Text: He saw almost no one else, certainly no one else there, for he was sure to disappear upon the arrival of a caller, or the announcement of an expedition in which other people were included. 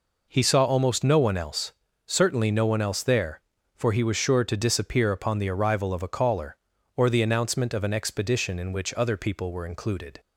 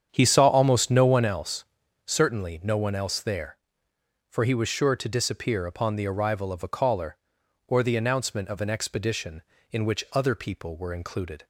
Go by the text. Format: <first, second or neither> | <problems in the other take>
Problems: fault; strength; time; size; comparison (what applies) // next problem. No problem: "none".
first | starts louder than the rest; strong; until 1.4 s; 8 dB